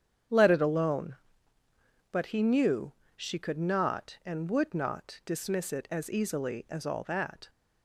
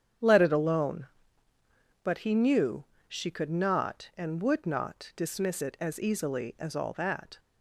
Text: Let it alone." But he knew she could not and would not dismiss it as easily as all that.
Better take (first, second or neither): neither